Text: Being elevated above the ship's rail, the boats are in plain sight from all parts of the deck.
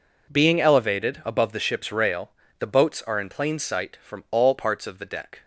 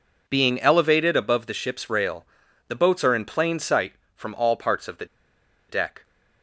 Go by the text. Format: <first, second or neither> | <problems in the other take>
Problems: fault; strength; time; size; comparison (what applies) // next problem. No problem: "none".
first | pauses between "the" and "deck"; noticeable; at 5.0 s; 0.64 s long